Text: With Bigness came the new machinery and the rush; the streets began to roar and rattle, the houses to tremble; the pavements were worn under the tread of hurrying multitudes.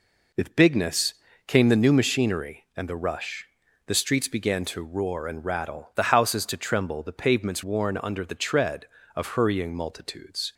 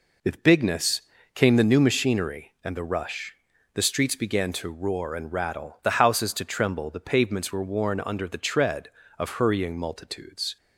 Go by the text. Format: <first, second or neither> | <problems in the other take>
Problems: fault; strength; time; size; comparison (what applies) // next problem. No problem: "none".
second | pauses between "Bigness" and "came"; slight; at 1.1 s; 0.34 s long; slight in the second // skips "were"; at 7.6 s